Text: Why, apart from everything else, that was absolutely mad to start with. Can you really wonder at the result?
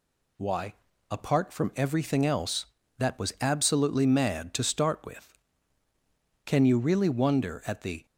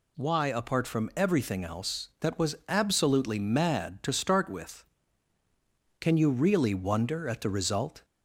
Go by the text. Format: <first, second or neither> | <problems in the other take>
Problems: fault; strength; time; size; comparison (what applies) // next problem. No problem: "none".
second | stops before "result"; at 8.0 s